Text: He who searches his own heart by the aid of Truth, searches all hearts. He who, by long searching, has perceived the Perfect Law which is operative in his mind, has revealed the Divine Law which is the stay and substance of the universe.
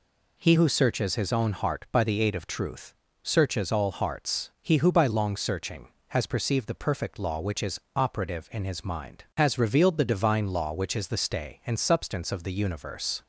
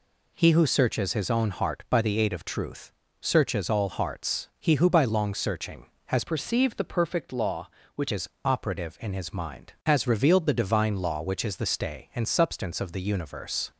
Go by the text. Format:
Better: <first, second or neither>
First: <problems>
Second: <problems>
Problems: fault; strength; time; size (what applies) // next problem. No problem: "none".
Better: first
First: pauses between "is" and "operative"; slight; at 7.7 s; 0.16 s long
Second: changes voice from "perceived" to "which"; from 6.2 to 8.1 s; 1.9 s long // pauses between "is" and "operative"; slight; at 8.2 s; 0.16 s long